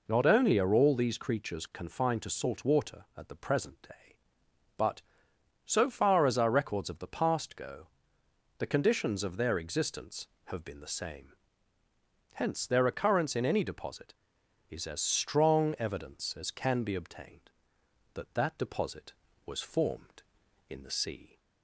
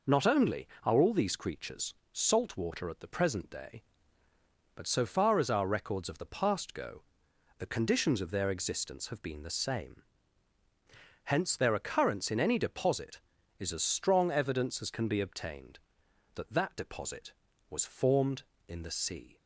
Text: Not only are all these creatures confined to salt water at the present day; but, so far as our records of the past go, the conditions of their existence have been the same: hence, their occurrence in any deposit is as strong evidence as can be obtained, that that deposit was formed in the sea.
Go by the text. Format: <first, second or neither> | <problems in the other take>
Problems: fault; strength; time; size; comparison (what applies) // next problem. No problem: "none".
first | skips "confined to"; at 2.0 s